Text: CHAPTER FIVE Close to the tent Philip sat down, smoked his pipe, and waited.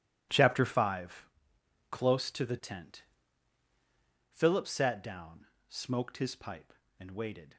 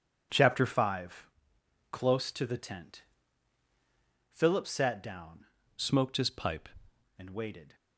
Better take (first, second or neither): first